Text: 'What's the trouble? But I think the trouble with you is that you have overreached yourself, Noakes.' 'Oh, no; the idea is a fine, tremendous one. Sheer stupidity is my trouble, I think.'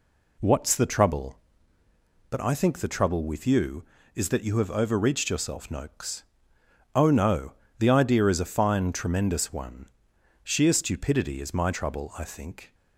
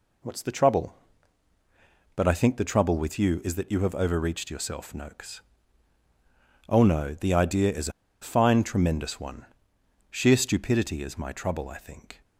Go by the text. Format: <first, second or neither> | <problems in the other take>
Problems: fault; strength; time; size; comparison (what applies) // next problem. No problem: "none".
first | pauses between "is" and "a"; slight; at 7.8 s; 0.32 s long